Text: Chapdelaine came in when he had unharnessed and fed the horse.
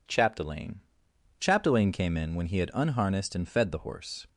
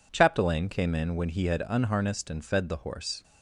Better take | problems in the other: second | says "Chapdelaine" twice; at 1.3 s

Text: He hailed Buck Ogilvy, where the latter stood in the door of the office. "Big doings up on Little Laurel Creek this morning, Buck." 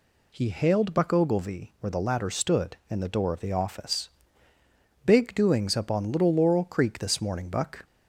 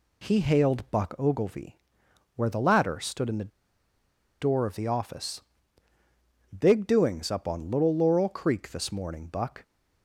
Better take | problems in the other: first | pauses between "the" and "door"; noticeable; at 3.5 s; 0.90 s long

